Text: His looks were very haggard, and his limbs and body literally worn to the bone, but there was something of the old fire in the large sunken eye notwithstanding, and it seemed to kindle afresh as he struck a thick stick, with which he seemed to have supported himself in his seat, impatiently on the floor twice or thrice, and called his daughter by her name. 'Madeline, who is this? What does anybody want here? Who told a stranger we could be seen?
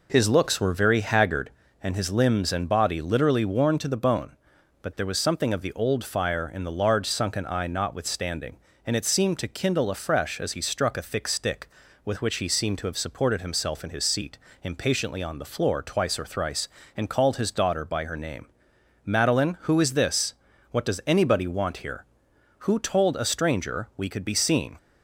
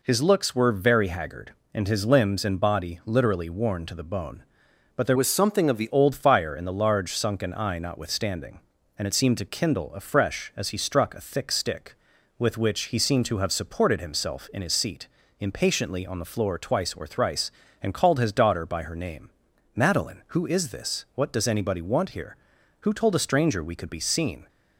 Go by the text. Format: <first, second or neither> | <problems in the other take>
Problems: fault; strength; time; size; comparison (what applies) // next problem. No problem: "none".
first | changes voice from "was" to "the"; from 5.1 to 5.8 s; 0.7 s long